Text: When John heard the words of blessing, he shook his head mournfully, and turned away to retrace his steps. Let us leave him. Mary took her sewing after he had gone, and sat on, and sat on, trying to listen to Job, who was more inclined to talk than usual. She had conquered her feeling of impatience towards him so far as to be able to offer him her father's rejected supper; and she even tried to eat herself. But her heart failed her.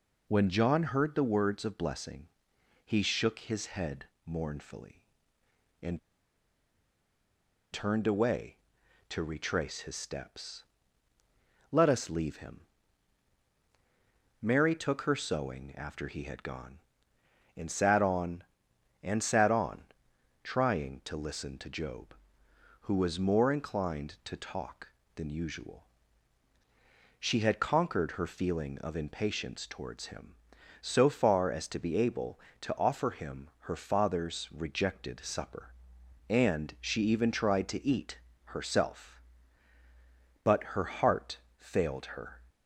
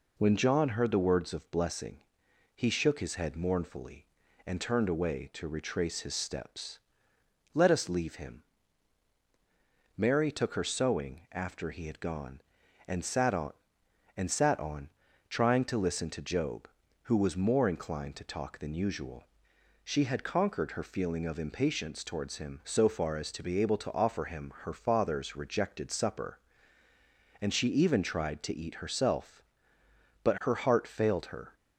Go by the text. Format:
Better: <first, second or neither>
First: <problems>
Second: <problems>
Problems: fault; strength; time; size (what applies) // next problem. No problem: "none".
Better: second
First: pauses between "head" and "mournfully"; slight; at 4.0 s; 0.20 s long // pauses between "and" and "turned"; strong; at 5.9 s; 1.7 s long // pauses between "eat" and "herself"; slight; at 38.1 s; 0.28 s long // pauses between "heart" and "failed"; slight; at 41.3 s; 0.18 s long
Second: none